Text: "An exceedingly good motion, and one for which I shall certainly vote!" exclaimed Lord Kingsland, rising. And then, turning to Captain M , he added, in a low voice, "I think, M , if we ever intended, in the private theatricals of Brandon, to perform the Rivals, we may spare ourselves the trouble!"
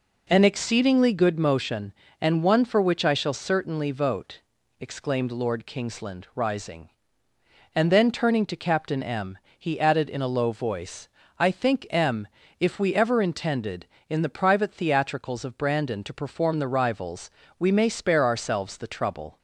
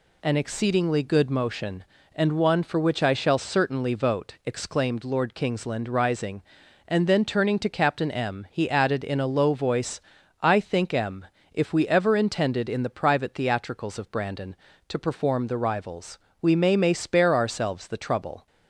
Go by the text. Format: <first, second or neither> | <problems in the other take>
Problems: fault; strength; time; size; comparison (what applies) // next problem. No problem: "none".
first | says "may" twice; at 16.7 s